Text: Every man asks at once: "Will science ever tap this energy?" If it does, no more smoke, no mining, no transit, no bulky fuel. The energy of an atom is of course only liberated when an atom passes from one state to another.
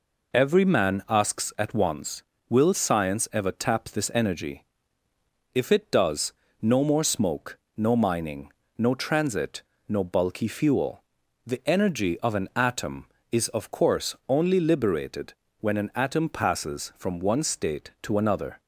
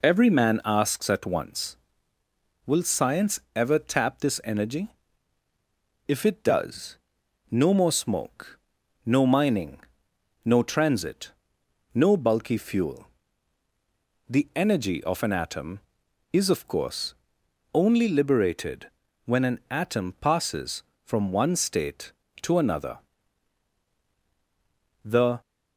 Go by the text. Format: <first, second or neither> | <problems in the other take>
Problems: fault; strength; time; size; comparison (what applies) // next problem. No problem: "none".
first | pauses between "science" and "ever"; slight; at 3.3 s; 0.16 s long // pauses between "course" and "only"; noticeable; at 17.1 s; 0.62 s long // pauses between "liberated" and "when"; at 18.8 s; 0.38 s long; slight in the first // goes on to say "The"; slight; from 25.0 s on; 0.36 s long